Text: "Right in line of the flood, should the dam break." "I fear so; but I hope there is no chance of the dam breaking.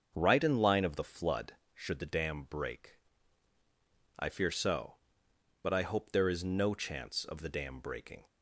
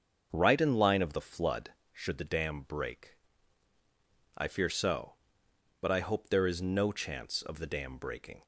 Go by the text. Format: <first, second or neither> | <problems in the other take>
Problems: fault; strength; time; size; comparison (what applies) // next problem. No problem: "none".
neither | starts louder than the rest; the same in both